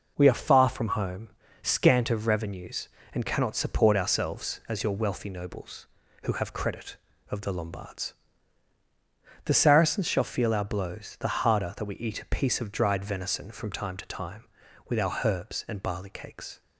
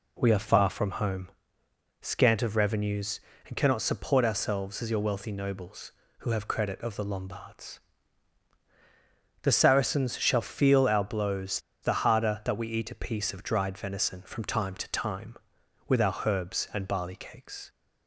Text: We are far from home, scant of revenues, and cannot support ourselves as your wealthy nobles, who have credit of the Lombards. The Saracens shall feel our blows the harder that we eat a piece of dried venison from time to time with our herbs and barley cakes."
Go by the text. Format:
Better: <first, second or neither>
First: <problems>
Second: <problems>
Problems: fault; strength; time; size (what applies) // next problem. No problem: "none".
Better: first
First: none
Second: pauses between "blows" and "the"; slight; at 11.5 s; 0.23 s long